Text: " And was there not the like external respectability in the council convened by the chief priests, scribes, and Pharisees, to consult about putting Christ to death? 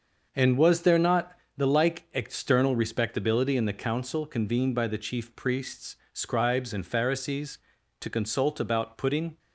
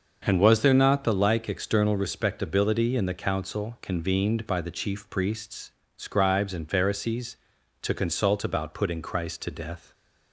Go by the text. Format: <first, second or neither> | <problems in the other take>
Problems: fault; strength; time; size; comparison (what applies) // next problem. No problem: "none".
second | starts louder than the rest; until 1.3 s; 6 dB; noticeable in the second // pauses between "not" and "the"; slight; at 1.3 s; 0.24 s long // stops before "Christ to death"; at 9.3 s